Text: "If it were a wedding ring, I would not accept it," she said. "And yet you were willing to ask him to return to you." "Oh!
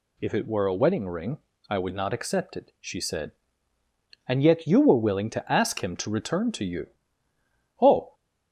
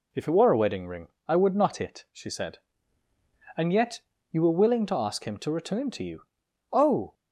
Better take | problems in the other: first | skips "accept"; at 1.7 s // pauses between "yet" and "you"; slight; at 4.0 s; 0.30 s long

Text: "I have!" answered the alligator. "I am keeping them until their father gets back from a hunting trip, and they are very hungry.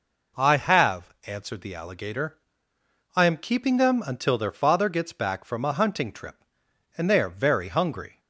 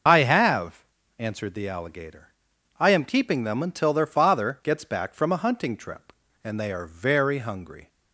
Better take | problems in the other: first | loses the start of "I"; at 0.0 s; 55 ms // starts louder than the rest; until 1.4 s; 6.5 dB

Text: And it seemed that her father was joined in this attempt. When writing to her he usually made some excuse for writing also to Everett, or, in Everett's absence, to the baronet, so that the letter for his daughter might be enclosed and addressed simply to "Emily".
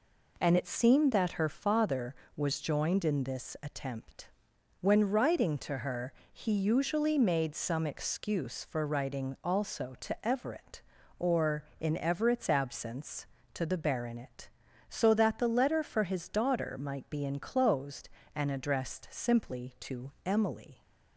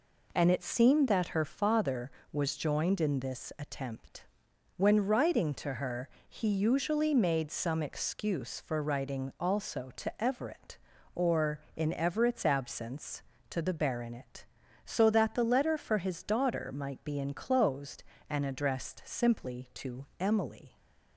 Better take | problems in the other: neither | pauses between "her" and "he"; slight; the same in both // pauses between "to" and "Emily"; slight; the same in both

